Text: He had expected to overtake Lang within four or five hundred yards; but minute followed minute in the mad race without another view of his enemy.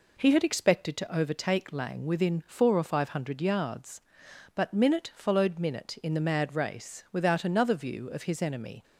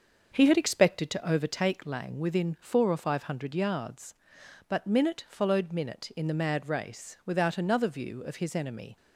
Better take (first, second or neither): first